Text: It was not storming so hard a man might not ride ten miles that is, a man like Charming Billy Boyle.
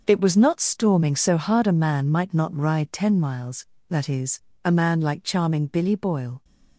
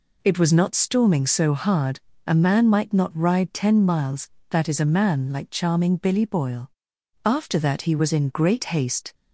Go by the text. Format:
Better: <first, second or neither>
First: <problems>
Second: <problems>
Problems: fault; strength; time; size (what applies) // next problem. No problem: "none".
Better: first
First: none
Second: pauses between "hard" and "a"; slight; at 1.9 s; 0.28 s long // goes on to say "After that he was in great haste"; strong; from 7.2 s on; 1.9 s long